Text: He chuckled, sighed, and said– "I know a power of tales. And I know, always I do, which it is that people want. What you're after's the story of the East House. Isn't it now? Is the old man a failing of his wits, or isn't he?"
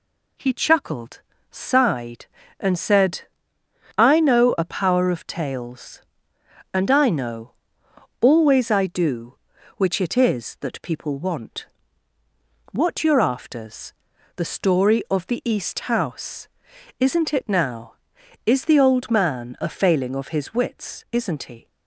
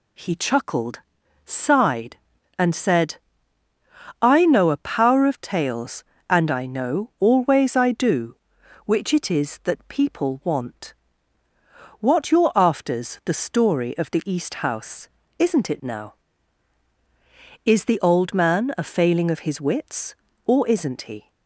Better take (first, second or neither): second